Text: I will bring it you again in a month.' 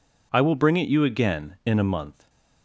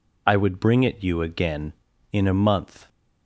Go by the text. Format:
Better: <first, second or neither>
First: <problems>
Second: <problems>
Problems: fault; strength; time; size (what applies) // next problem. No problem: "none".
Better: first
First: none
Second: says "would" for "will"; at 0.3 s